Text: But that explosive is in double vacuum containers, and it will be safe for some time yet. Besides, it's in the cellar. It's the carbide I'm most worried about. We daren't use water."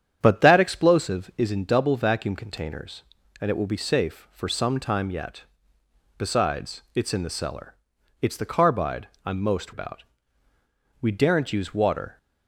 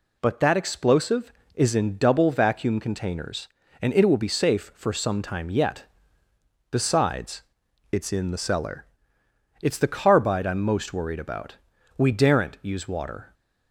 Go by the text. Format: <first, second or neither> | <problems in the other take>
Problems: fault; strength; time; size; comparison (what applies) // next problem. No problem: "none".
second | starts louder than the rest; strong; until 1.2 s; 9 dB // pauses between "carbide" and "I'm"; slight; at 9.0 s; 0.18 s long // skips "worried"; at 9.7 s